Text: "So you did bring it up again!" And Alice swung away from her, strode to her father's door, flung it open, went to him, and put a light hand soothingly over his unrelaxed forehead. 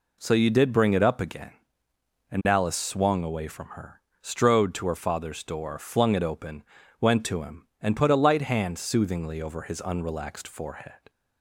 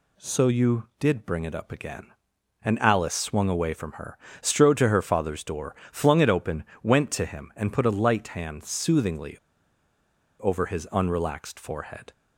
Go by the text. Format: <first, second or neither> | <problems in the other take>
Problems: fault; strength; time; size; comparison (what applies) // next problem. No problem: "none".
first | pauses between "soothingly" and "over"; at 9.3 s; 1.0 s long